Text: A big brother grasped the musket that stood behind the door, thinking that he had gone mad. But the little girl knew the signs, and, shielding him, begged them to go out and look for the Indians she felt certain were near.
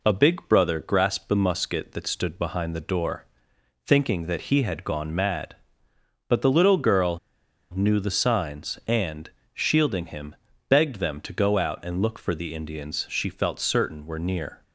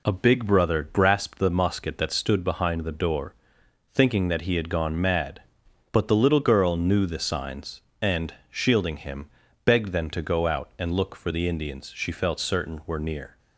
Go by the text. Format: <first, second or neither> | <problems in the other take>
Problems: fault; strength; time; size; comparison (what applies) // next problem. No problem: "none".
second | pauses between "girl" and "knew"; noticeable; at 7.1 s; 0.55 s long